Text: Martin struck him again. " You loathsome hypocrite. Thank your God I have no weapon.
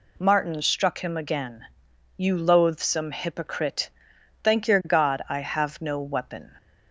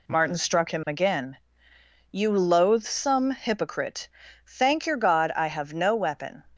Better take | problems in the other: neither | none

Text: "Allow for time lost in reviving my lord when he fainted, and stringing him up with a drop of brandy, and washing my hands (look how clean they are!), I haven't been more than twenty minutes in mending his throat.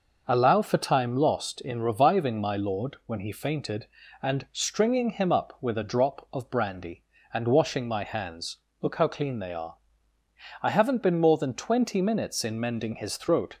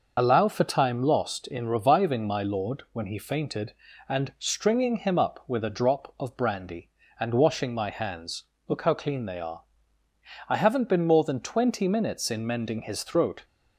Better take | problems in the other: first | loses the start of "Allow"; at 0.1 s; 50 ms

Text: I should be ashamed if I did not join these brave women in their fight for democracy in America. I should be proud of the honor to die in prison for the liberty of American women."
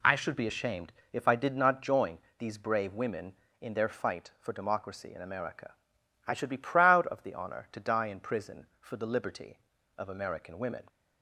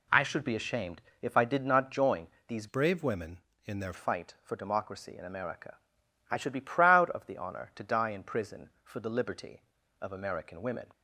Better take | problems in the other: first | pauses between "ashamed" and "if"; slight; at 1.0 s; 0.18 s long; slight in the first // pauses between "join" and "these"; slight; at 2.2 s; 0.20 s long; slight in the first // changes voice from "brave" to "their"; from 2.6 to 3.9 s; 1.3 s long

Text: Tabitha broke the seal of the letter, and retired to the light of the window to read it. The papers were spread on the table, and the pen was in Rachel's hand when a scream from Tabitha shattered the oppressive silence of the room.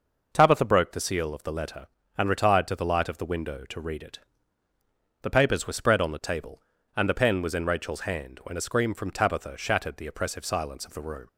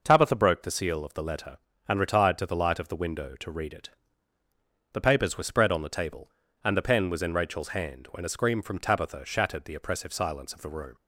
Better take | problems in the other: neither | none

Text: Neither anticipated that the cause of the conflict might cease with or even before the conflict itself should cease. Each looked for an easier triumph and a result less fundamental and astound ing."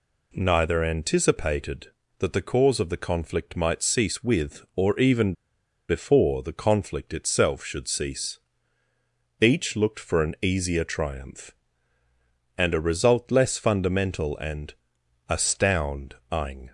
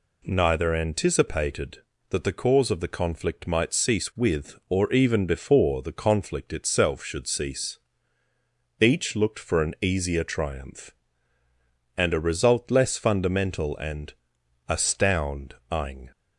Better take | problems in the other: second | pauses between "even" and "before"; noticeable; at 5.3 s; 0.56 s long // pauses between "and" and "astound"; noticeable; at 14.7 s; 0.56 s long; noticeable in the second // pauses between "astound" and "ing"; slight; at 16.1 s; 0.18 s long; slight in the second

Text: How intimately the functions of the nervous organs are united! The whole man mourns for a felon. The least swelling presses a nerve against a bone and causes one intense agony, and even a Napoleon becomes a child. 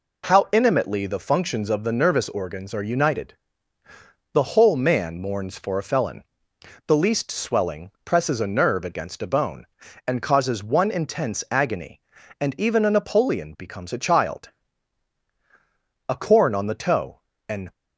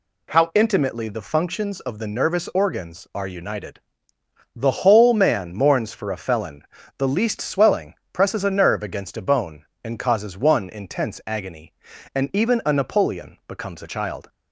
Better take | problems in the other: second | pauses between "swelling" and "presses"; slight; at 7.9 s; 0.16 s long; slight in the second // goes on to say "A corn on the toe an"; from 16.0 s on; 1.6 s long

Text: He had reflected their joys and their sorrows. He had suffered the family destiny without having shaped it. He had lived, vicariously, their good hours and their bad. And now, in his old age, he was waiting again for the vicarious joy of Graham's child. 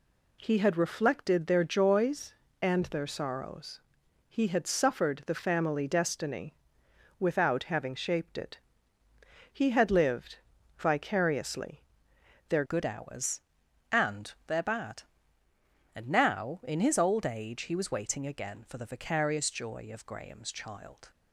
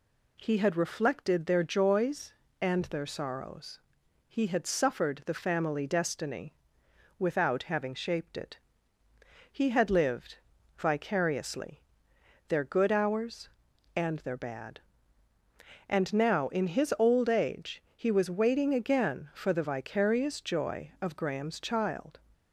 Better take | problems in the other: second | pauses between "destiny" and "without"; noticeable; at 6.5 s; 0.64 s long; noticeable in the second // changes voice at "good"; from 12.6 s on; 8.5 s long

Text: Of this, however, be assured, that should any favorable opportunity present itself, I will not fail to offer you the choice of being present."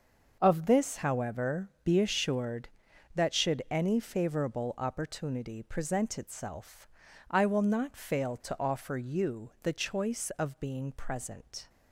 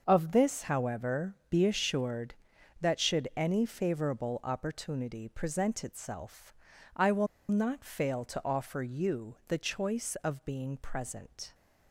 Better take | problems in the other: first | starts louder than the rest; until 1.0 s; 6 dB; noticeable in the first // pauses between "will" and "not"; slight; at 7.2 s; 0.23 s long

